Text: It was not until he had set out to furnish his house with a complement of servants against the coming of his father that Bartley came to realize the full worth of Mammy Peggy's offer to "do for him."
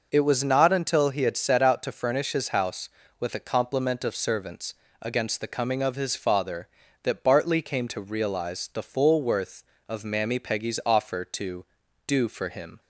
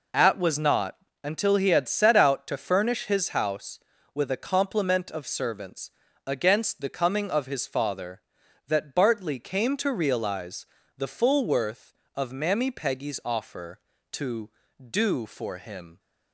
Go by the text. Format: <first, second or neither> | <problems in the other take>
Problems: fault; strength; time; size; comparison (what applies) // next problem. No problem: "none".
first | says "At" for "It"; at 0.1 s // pauses between "not" and "until"; slight; at 0.9 s; 0.26 s long // pauses between "servants" and "against"; slight; at 5.9 s; 0.34 s long; slight in the first // pauses between "realize" and "the"; slight; at 10.6 s; 0.32 s long